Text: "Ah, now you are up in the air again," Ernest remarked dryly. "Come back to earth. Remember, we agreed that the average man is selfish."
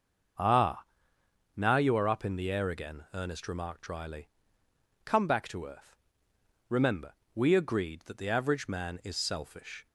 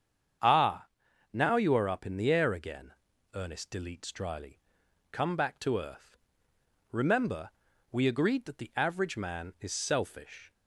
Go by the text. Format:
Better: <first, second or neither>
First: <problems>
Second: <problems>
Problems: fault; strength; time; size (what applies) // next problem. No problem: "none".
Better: first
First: starts louder than the rest; until 2.0 s; 6 dB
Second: starts louder than the rest; strong; until 1.8 s; 8 dB // says "deletes" for "remarked"; at 3.6 s